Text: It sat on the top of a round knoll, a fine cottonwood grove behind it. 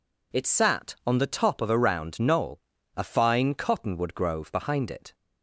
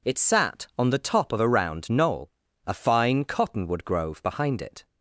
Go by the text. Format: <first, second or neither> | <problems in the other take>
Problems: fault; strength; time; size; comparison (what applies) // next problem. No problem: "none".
neither | none